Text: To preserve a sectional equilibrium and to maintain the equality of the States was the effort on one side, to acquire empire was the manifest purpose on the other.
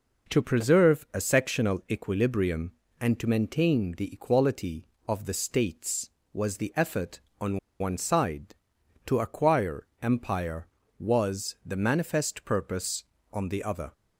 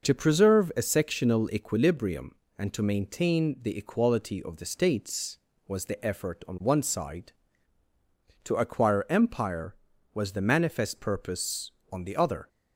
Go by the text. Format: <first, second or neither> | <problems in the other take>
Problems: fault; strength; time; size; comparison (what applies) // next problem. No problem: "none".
second | pauses between "on" and "one"; slight; at 7.5 s; 0.20 s long